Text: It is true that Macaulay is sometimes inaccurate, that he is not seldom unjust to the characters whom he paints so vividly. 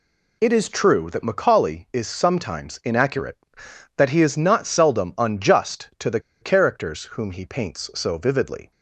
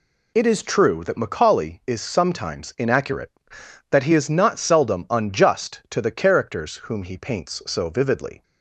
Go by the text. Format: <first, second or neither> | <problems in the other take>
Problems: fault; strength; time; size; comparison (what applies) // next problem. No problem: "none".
second | pauses between "the" and "characters"; slight; at 6.1 s; 0.21 s long